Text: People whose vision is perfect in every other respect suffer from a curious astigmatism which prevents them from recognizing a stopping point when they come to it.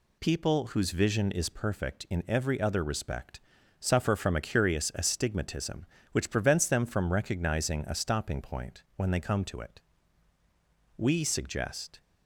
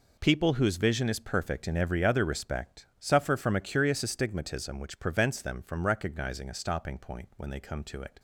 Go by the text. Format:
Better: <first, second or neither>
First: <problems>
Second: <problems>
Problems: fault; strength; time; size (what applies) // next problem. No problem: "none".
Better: second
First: pauses between "respect" and "suffer"; at 3.3 s; 0.40 s long // goes on to say "We suggest"; noticeable; from 10.9 s on; 1.0 s long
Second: none